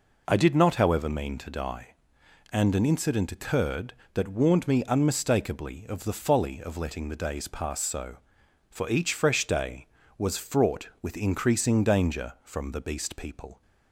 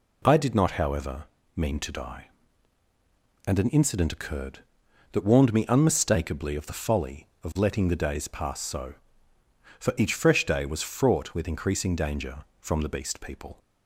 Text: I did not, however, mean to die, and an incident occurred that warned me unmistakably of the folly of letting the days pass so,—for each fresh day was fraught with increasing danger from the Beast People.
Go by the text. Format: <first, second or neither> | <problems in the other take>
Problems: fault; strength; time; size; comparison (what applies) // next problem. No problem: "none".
neither | none